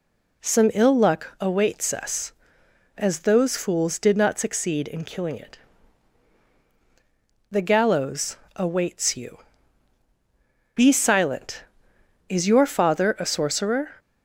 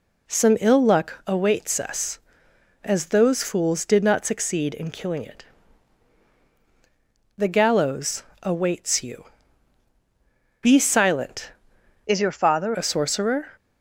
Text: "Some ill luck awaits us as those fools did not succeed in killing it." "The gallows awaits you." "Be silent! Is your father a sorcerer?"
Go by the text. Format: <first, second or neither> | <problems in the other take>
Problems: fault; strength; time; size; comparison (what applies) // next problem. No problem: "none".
first | pauses between "gallows" and "awaits"; slight; at 8.2 s; 0.18 s long; slight in the first // changes voice from "Is" to "father"; from 12.0 to 12.7 s; 0.7 s long